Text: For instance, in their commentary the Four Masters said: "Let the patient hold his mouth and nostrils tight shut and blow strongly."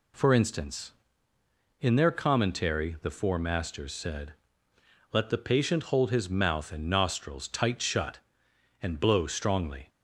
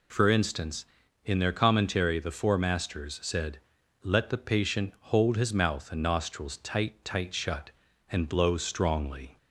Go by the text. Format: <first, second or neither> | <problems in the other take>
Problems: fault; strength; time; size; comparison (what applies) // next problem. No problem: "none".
first | says "tight" twice; at 7.0 s